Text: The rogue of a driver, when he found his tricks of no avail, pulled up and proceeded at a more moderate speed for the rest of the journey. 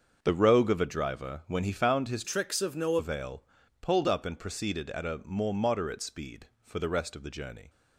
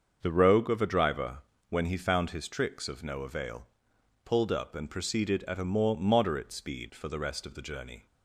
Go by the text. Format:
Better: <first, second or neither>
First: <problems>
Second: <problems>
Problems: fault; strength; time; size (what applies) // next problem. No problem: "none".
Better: second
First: starts louder than the rest; until 1.2 s; 6.5 dB // changes voice from "tricks" to "no"; from 2.2 to 2.9 s; 0.7 s long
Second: starts louder than the rest; until 1.2 s; 7 dB